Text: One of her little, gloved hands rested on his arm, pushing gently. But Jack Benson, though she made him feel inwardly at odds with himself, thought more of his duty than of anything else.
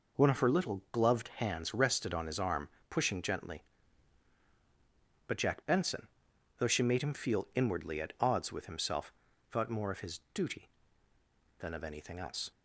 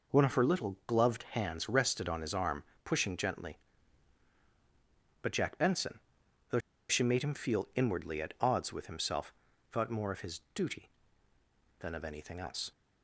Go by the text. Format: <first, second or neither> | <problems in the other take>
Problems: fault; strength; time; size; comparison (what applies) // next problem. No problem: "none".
first | pauses between "though" and "she"; slight; at 6.5 s; 0.30 s long